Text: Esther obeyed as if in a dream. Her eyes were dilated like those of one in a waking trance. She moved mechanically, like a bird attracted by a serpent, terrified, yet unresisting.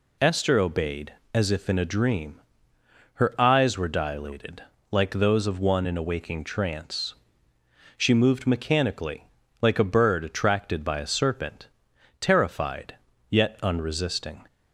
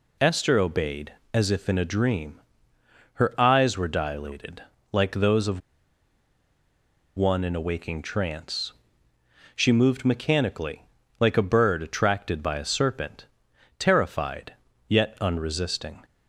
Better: first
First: pauses between "dilated" and "like"; slight; at 4.6 s; 0.28 s long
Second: pauses between "dilated" and "like"; slight; at 4.6 s; 0.30 s long // pauses between "of" and "one"; strong; at 5.5 s; 1.5 s long

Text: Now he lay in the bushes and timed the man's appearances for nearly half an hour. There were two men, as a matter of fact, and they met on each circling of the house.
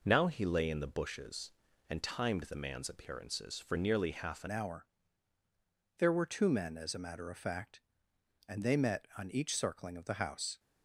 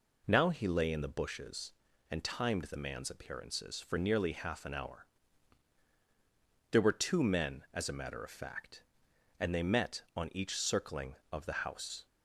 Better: second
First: changes voice at "hour"; from 4.4 s on; 6.1 s long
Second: none

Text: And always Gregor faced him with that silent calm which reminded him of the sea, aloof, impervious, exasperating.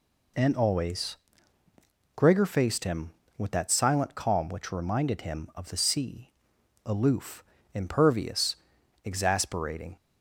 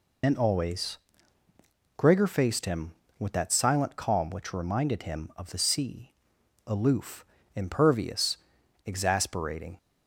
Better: first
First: pauses between "always" and "Gregor"; at 1.1 s; 1.0 s long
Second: loses the start of "And"; at 0.2 s; 65 ms // pauses between "always" and "Gregor"; at 0.9 s; 1.0 s long

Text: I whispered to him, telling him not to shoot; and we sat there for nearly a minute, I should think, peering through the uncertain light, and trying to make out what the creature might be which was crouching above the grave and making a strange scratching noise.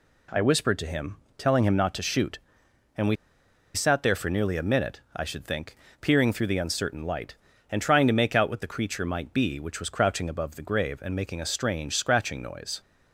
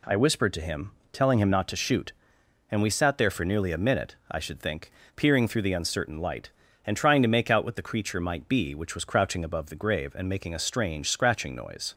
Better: second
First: pauses between "we" and "sat"; noticeable; at 3.1 s; 0.59 s long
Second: none

